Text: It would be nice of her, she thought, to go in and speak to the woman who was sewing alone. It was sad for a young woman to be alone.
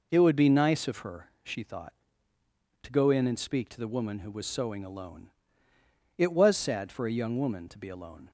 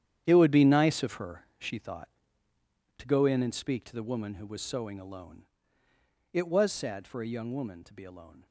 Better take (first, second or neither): first